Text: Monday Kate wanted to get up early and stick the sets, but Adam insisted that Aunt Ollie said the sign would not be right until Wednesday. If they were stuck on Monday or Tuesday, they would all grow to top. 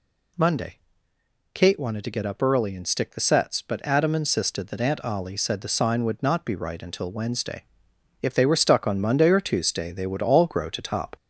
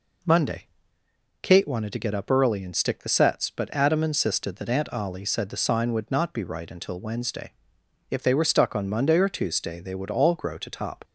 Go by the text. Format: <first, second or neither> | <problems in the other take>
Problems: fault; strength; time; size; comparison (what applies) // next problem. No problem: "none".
second | gets louder; slight; throughout; 3 dB // pauses between "Monday" and "Kate"; noticeable; at 0.7 s; 0.74 s long; noticeable in the second